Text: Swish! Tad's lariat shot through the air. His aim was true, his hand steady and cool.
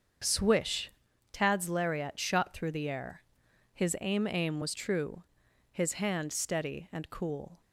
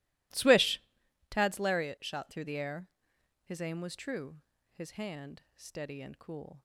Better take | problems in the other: second | starts louder than the rest; until 1.6 s; 7 dB // says "aim" twice; at 4.3 s

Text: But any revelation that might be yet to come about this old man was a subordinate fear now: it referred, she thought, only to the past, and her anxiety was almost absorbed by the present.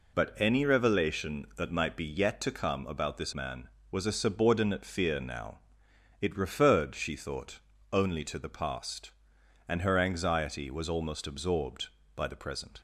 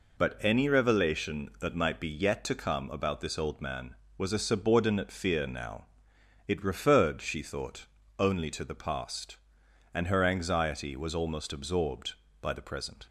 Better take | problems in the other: second | skips "old"; at 3.3 s

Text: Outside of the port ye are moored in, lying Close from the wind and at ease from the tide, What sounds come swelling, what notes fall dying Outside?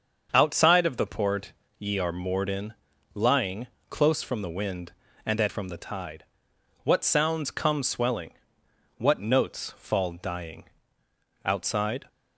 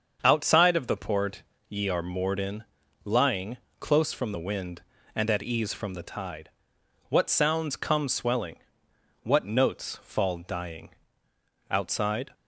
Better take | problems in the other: second | starts louder than the rest; until 1.3 s; 6.5 dB; also in the second // pauses between "port" and "ye"; slight; at 1.5 s; 0.28 s long; slight in the second // pauses between "lying" and "Close"; slight; at 3.6 s; 0.22 s long; slight in the second // skips "ease"; at 5.4 s // pauses between "dying" and "Outside"; noticeable; at 10.6 s; 0.80 s long; noticeable in the second

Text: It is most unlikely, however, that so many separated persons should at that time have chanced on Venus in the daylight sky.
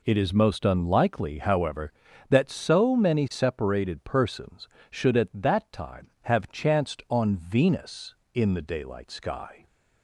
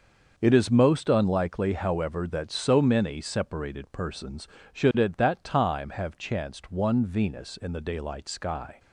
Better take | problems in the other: first | starts louder than the rest; until 1.3 s; 6.5 dB // says "one" for "on"; at 6.7 s

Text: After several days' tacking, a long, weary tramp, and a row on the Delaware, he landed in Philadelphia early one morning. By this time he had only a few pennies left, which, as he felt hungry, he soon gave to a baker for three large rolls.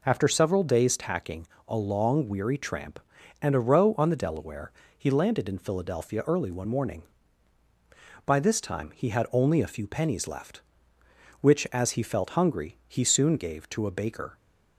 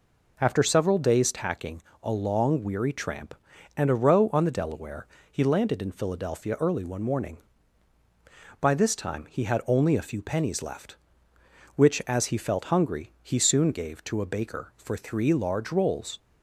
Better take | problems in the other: second | stops before "for three large rolls"; at 14.3 s

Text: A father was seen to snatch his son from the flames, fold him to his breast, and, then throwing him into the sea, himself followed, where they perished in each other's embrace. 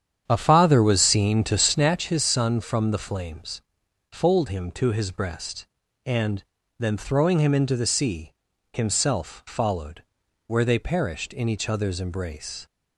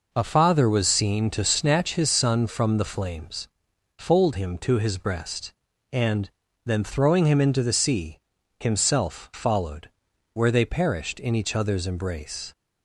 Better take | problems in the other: second | starts louder than the rest; strong; until 2.0 s; 8.5 dB

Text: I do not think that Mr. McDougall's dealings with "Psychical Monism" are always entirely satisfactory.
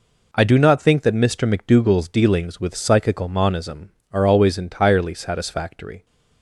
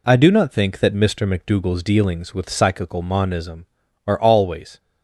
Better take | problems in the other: first | stops before "entirely satisfactory"; at 4.7 s

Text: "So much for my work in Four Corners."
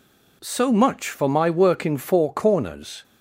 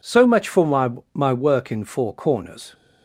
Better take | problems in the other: first | says "my" twice; at 1.1 s

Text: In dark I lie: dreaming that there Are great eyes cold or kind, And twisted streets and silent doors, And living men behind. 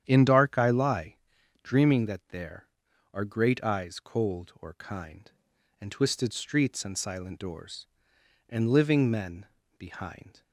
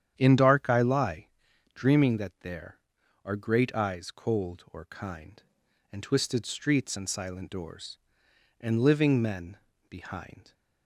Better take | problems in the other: neither | starts louder than the rest; strong; the same in both // pauses between "men" and "behind"; slight; the same in both

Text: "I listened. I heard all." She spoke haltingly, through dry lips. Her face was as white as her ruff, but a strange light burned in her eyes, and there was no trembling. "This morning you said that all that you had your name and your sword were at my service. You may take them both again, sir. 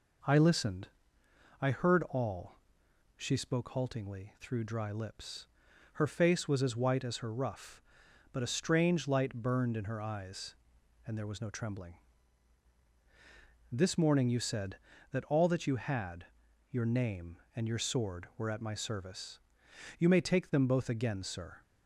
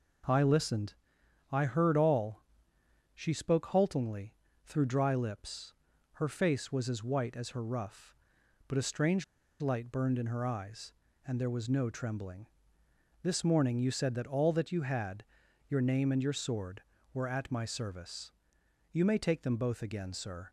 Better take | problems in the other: first | pauses between "strange" and "light"; at 9.2 s; 0.37 s long // pauses between "had" and "your"; at 15.2 s; 0.44 s long; also in the first

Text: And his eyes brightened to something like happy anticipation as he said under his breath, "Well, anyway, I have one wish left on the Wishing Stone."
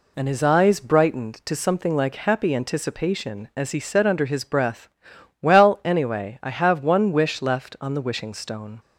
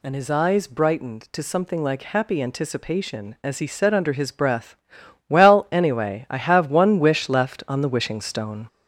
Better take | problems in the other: first | gets louder; noticeable; throughout; 5 dB

